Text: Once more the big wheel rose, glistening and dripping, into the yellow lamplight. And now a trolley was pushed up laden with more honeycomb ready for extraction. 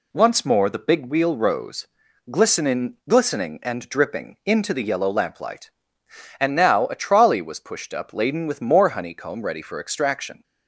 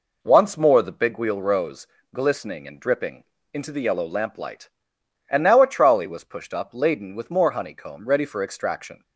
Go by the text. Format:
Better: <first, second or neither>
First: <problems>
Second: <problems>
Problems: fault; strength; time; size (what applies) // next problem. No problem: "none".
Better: second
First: says "glistening" twice; at 3.0 s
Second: none